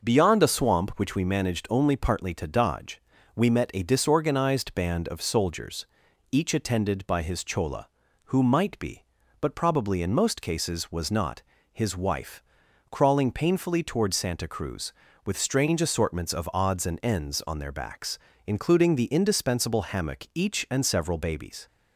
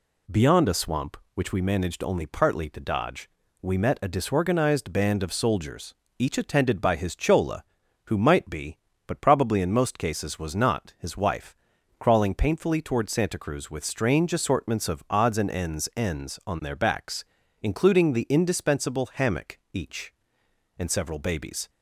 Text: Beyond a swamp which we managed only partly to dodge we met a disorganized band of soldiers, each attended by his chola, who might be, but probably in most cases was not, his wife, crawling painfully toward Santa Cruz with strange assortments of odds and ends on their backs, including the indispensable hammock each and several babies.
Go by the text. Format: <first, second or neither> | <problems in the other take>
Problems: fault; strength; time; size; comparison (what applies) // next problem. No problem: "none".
first | pauses between "dodge" and "we"; slight; at 3.2 s; 0.32 s long; slight in the first // says "ends" twice; at 15.9 s